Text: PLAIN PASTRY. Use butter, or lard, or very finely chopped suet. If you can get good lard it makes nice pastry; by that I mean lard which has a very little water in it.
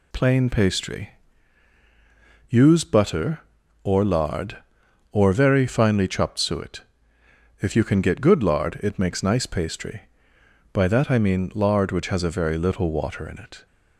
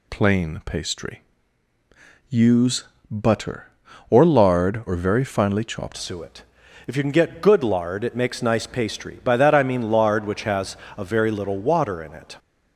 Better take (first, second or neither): first